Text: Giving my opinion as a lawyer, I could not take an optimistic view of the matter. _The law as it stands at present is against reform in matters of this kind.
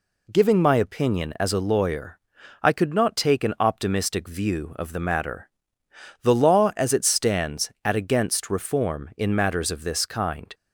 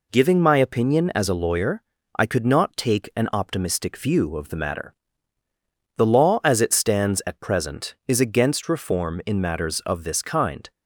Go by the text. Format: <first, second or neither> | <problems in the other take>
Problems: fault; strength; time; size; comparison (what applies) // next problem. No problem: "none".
second | skips "present is"; at 7.9 s